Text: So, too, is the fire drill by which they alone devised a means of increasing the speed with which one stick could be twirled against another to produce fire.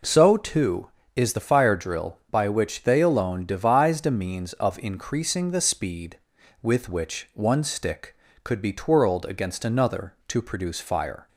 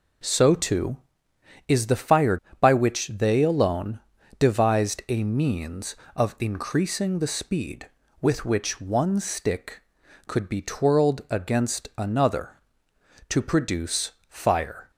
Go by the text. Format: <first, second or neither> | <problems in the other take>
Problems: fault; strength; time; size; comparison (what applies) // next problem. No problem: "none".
first | skips "drill"; at 2.4 s // pauses between "alone" and "devised"; at 4.0 s; 0.40 s long // pauses between "produce" and "fire"; slight; at 14.1 s; 0.18 s long